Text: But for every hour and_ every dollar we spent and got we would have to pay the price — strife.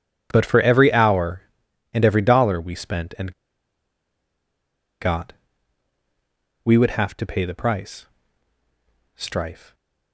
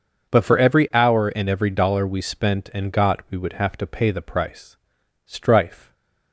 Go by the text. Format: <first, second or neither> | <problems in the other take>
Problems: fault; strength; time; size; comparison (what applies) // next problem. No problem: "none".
second | pauses between "and" and "got"; strong; at 3.3 s; 1.6 s long // pauses between "got" and "we"; strong; at 5.3 s; 1.3 s long